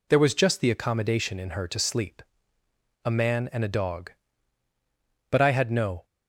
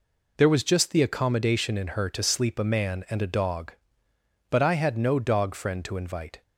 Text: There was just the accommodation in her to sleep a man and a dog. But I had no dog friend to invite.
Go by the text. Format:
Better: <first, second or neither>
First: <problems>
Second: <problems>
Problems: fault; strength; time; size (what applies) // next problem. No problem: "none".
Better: second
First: pauses between "sleep" and "a"; noticeable; at 2.2 s; 0.86 s long // stops before "dog friend to invite"; at 6.0 s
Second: none